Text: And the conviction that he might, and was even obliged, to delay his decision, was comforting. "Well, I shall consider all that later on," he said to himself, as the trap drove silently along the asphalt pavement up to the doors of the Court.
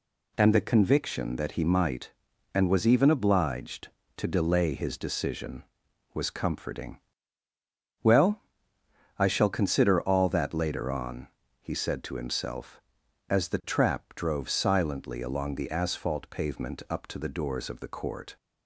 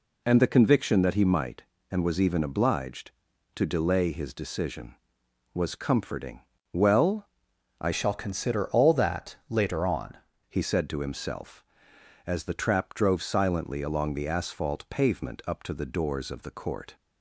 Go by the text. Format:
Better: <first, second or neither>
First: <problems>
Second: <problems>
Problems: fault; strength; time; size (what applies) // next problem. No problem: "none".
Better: first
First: none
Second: changes voice from "shall" to "on"; from 7.9 to 10.1 s; 2.2 s long